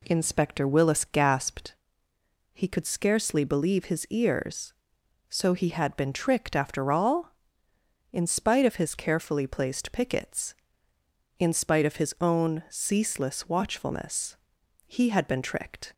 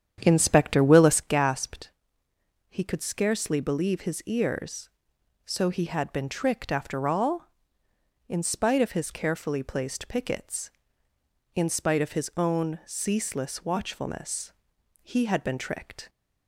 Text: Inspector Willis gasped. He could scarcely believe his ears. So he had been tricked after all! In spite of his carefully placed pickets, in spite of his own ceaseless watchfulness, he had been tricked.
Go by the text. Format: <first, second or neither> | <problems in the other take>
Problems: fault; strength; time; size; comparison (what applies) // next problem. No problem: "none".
first | starts louder than the rest; strong; until 1.4 s; 9 dB